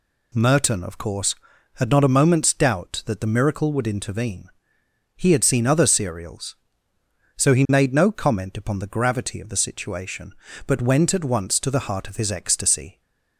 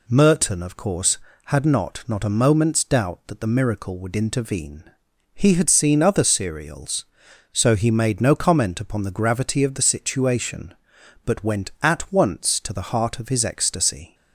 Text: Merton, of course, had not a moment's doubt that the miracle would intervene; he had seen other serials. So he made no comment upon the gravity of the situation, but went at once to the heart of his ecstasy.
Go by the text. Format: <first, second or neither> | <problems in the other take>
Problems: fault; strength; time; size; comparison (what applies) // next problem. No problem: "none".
first | says "not" twice; at 2.0 s